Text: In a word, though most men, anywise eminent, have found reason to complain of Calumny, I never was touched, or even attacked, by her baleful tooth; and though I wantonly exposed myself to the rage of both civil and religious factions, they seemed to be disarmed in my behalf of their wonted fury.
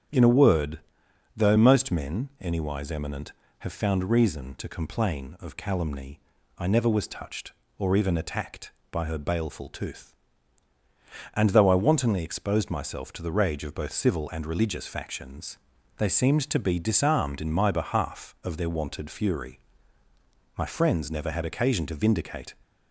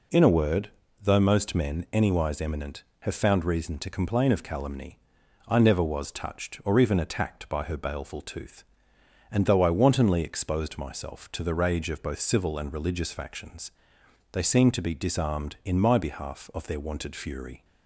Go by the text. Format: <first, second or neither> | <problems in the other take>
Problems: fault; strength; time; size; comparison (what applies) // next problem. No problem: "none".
second | starts louder than the rest; strong; until 1.7 s; 9 dB // goes on to say "My friends never had occasion to vindicate"; strong; from 20.5 s on; 1.9 s long